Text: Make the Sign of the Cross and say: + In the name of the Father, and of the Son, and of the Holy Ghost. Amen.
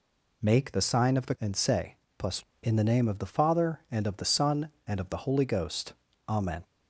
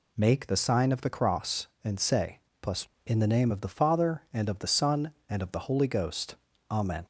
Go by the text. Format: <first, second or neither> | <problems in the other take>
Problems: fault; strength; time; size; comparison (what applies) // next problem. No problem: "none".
second | skips "Cross"; at 1.3 s